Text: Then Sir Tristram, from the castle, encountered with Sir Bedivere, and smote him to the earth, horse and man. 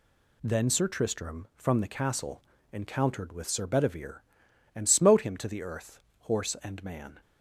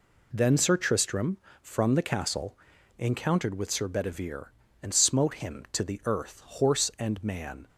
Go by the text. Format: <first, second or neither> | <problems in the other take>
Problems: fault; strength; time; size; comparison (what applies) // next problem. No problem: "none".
neither | none